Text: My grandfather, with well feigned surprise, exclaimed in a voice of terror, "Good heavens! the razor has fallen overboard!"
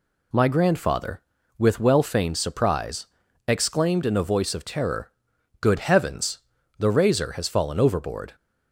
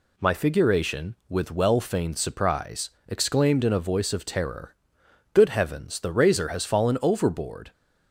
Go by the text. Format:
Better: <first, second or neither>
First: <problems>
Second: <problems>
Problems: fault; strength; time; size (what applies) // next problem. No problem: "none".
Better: first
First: none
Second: says "figuration" for "grandfather"; at 0.3 s